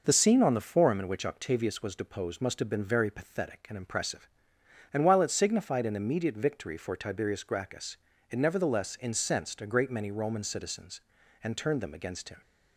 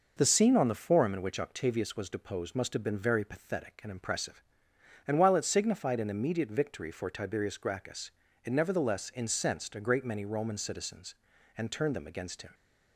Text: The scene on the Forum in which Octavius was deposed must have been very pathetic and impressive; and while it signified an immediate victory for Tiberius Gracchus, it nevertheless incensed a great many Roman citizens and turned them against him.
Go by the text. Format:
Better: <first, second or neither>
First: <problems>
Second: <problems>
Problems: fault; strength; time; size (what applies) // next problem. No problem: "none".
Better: neither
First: none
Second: none